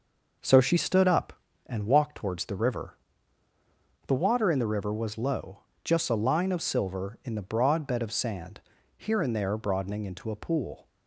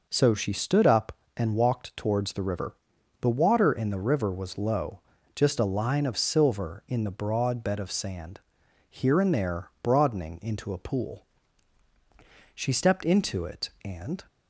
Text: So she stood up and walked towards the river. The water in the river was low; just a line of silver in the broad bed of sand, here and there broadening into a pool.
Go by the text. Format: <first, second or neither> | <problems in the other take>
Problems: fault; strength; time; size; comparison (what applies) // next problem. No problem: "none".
first | goes on to say "She stepped into it and"; strong; from 12.5 s on; 1.6 s long